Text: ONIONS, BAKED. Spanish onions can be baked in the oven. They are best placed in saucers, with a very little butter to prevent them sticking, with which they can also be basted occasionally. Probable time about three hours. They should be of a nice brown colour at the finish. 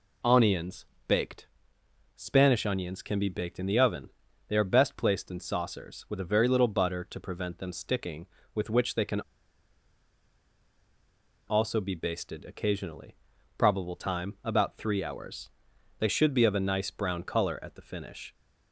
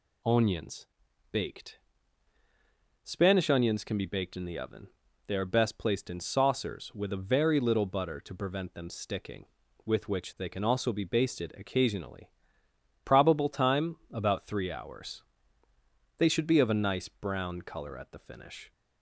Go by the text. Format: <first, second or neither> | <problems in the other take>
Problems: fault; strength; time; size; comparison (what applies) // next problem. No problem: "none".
second | pauses between "can" and "also"; strong; at 9.2 s; 2.2 s long